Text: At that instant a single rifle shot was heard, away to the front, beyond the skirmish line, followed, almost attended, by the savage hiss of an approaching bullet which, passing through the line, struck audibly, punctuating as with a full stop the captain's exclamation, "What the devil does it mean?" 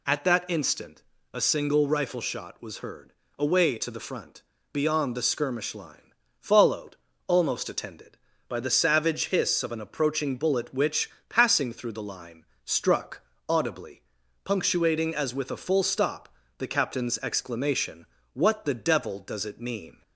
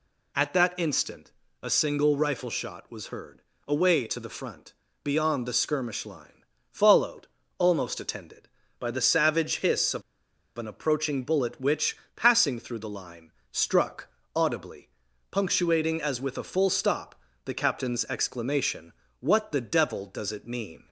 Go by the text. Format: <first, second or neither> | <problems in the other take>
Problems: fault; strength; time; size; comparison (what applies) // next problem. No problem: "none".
first | pauses between "instant" and "a"; slight; at 1.3 s; 0.32 s long; slight in the first // pauses between "of" and "an"; noticeable; at 10.0 s; 0.56 s long // pauses between "struck" and "audibly"; slight; at 14.0 s; 0.26 s long; slight in the first // pauses between "stop" and "the"; slight; at 17.1 s; 0.30 s long; slight in the first